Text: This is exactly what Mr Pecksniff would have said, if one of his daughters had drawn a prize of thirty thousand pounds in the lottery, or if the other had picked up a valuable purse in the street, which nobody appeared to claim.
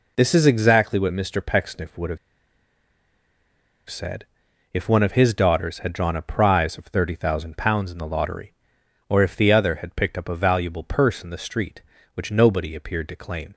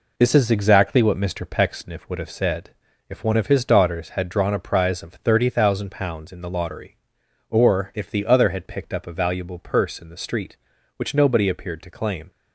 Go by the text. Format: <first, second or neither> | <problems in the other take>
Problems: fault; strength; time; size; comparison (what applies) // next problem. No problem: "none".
second | pauses between "have" and "said"; strong; at 2.1 s; 1.7 s long